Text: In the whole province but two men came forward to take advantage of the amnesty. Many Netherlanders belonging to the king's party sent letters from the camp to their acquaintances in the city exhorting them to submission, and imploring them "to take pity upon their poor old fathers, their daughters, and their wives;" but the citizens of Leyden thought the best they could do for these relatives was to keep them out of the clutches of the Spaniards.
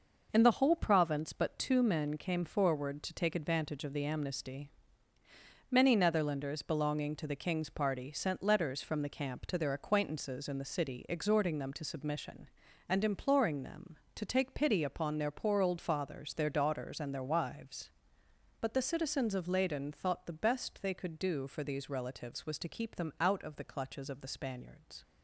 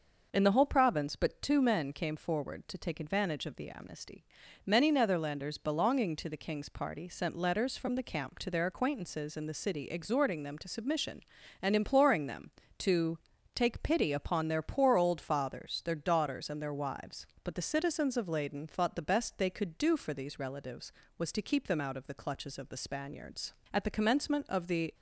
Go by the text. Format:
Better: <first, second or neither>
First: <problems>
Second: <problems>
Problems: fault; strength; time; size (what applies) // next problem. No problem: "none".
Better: first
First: none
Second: pauses between "to" and "take"; at 13.1 s; 0.38 s long // goes on to say "At the commencement of the"; noticeable; from 23.7 s on; 1.2 s long